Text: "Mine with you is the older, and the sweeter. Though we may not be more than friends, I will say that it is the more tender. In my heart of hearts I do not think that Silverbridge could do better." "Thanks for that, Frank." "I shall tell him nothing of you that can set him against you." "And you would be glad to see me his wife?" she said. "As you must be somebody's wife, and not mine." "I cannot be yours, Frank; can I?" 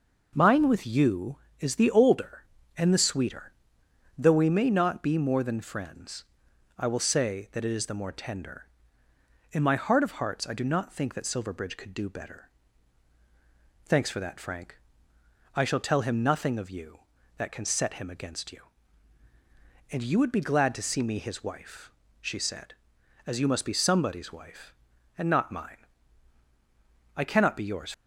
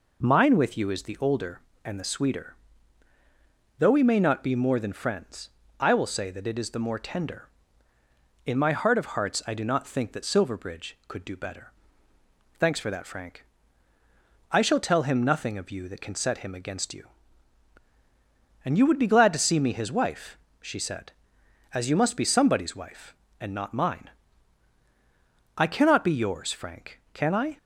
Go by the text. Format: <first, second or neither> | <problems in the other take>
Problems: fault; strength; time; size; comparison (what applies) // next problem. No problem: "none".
second | stops before "Frank can I"; at 27.9 s